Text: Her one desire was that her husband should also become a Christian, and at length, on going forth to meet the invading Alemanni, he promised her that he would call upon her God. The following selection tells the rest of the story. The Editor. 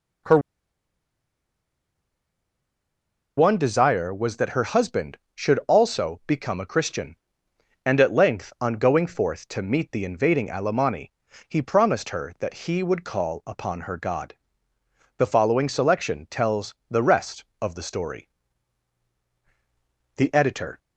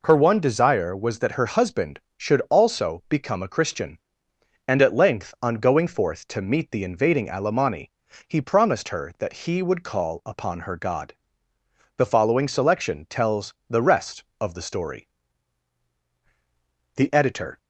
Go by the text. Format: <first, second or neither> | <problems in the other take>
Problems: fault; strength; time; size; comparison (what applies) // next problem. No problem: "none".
second | pauses between "Her" and "one"; strong; at 0.3 s; 2.9 s long